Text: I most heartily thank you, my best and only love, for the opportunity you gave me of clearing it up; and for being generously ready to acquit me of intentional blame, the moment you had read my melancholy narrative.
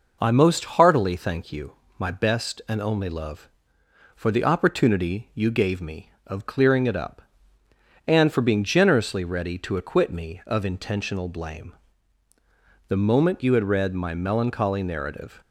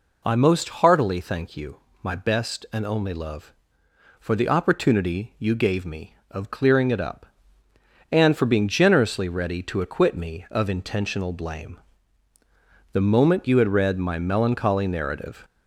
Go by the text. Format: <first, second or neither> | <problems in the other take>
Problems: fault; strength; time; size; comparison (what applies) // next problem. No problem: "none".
first | gets louder; slight; throughout; 3.5 dB